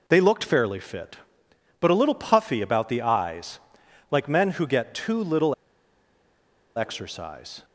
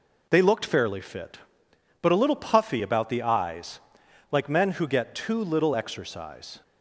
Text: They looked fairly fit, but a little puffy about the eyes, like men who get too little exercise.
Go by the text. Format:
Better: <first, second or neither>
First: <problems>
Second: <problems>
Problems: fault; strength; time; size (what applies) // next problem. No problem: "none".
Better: second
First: pauses between "little" and "exercise"; at 5.5 s; 1.2 s long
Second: none